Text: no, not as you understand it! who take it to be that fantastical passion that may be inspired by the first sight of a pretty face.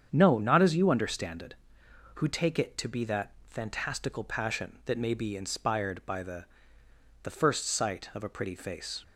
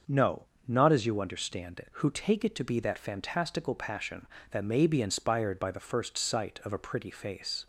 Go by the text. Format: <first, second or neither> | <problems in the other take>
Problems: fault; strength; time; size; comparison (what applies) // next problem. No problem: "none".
second | starts louder than the rest; strong; until 1.1 s; 7.5 dB; also in the second // pauses between "that" and "fantastical"; slight; at 3.3 s; 0.17 s long // says "the" twice; at 7.2 s